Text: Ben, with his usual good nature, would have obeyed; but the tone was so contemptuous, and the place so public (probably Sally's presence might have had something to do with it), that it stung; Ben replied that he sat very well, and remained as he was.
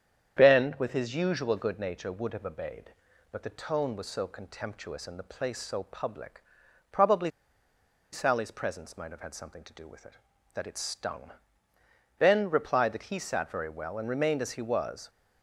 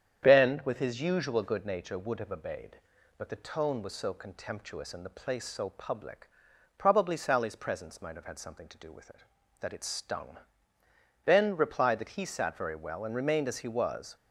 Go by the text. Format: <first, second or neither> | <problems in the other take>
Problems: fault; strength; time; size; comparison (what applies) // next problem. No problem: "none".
second | starts louder than the rest; strong; until 1.4 s; 8.5 dB; strong in the second // pauses between "probably" and "Sally's"; noticeable; at 7.3 s; 0.83 s long